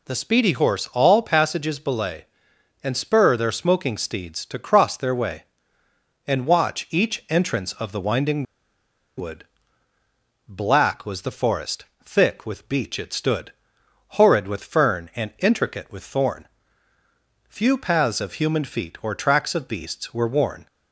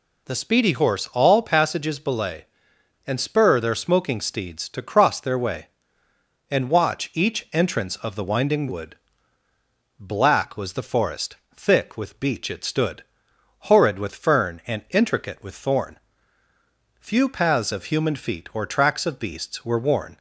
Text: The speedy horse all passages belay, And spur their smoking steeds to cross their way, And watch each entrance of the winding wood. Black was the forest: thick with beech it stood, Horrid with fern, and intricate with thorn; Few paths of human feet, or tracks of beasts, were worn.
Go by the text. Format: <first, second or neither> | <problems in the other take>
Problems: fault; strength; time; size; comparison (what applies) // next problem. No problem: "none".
second | pauses between "winding" and "wood"; noticeable; at 8.4 s; 0.73 s long